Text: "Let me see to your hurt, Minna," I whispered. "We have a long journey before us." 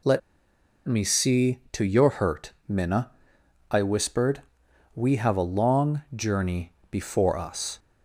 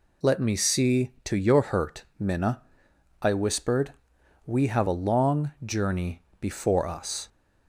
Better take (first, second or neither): second